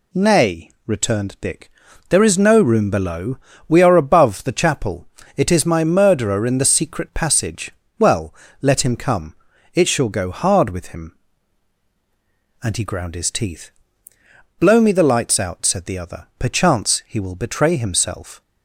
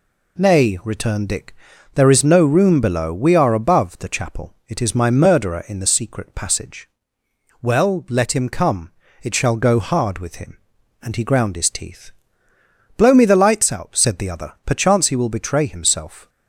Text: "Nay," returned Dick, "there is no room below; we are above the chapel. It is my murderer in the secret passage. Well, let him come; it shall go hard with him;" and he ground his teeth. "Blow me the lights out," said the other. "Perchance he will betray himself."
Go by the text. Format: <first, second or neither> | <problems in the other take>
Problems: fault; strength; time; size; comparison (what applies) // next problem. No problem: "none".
neither | none